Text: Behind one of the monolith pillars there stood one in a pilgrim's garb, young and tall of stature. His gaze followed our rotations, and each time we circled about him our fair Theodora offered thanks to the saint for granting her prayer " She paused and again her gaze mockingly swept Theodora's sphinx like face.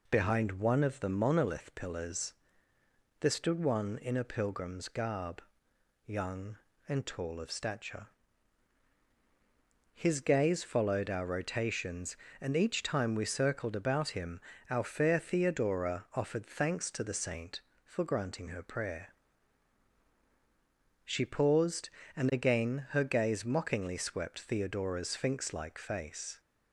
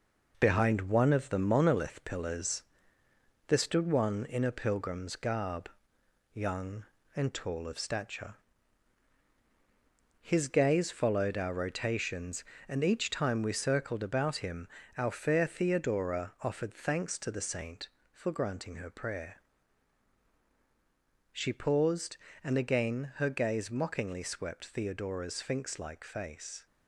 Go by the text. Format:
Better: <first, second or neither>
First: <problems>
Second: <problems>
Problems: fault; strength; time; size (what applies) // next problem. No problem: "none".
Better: first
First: pauses between "pillars" and "there"; noticeable; at 2.3 s; 0.88 s long // pauses between "him" and "our"; slight; at 14.3 s; 0.32 s long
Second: gets quieter; strong; throughout; 10 dB // pauses between "pillars" and "there"; noticeable; at 2.6 s; 0.86 s long // pauses between "him" and "our"; slight; at 14.6 s; 0.32 s long